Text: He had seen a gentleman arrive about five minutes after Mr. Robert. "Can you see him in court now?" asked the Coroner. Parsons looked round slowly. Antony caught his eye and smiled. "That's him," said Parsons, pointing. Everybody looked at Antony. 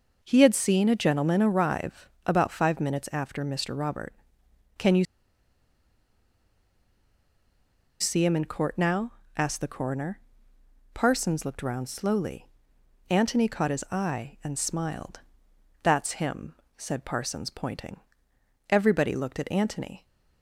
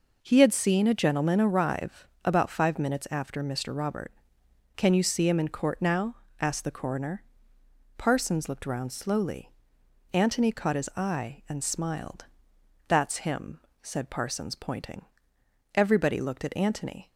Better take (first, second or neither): second